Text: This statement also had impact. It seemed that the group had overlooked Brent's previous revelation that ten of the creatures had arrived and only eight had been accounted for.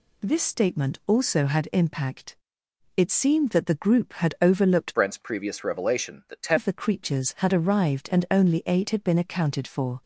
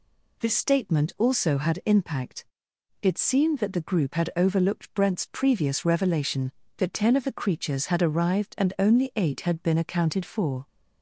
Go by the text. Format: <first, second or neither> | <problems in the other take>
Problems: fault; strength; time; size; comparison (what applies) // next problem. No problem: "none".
second | changes voice from "Brent's" to "ten"; from 4.9 to 6.5 s; 1.6 s long